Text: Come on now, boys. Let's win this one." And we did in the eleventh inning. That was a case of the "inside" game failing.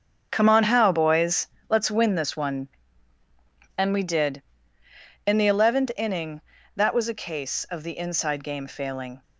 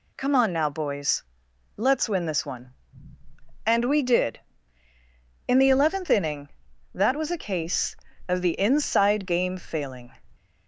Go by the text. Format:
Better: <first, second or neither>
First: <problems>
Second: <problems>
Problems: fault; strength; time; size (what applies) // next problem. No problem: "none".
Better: second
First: starts louder than the rest; until 1.3 s; 7 dB // says "how" for "now"; at 0.6 s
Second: none